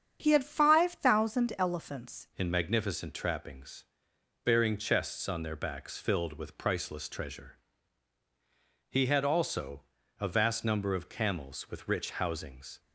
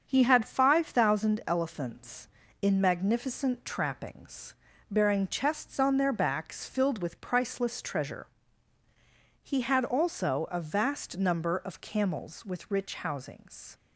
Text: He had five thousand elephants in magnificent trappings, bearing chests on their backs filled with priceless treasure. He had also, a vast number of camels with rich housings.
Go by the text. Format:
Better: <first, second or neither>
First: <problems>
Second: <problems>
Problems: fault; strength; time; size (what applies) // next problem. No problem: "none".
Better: second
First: starts louder than the rest; strong; until 1.2 s; 8 dB // changes voice at "in"; from 2.3 s on; 10.5 s long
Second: starts louder than the rest; until 1.1 s; 7 dB